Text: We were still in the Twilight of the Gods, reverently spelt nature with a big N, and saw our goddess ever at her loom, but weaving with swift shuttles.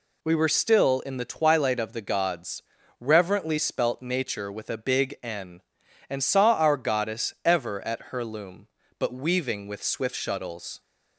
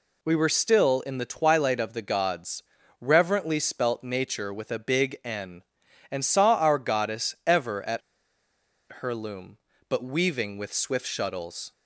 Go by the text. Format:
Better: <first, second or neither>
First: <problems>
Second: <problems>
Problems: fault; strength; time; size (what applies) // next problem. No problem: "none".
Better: first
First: none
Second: pauses between "at" and "her"; at 8.0 s; 1.0 s long